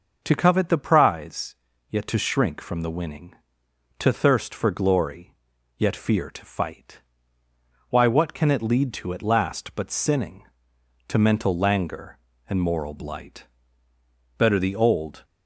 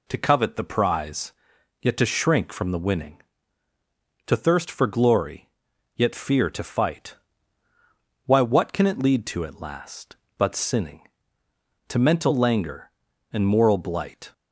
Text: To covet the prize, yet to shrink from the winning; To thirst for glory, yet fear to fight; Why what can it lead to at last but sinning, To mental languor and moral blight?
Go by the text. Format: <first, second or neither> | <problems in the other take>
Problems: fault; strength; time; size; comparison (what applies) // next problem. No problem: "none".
second | starts louder than the rest; until 1.2 s; 6 dB // goes on to say "Better the old"; noticeable; from 14.3 s on; 0.86 s long